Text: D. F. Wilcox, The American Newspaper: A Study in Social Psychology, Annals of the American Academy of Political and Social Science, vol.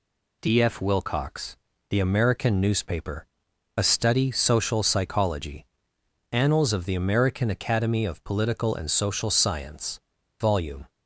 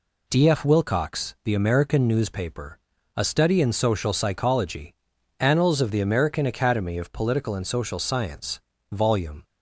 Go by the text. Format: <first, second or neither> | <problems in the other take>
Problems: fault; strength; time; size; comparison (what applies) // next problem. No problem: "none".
second | skips "in"; at 4.3 s